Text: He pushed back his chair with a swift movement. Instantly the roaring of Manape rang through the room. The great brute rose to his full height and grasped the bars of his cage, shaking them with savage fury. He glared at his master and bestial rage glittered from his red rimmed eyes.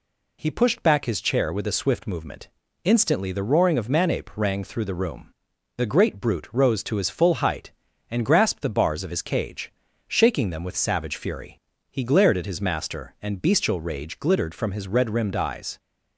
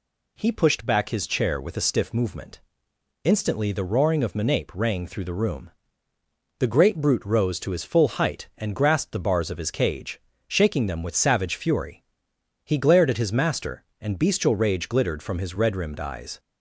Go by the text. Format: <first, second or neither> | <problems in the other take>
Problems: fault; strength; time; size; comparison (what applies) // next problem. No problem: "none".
first | says "stiff" for "swift"; at 1.8 s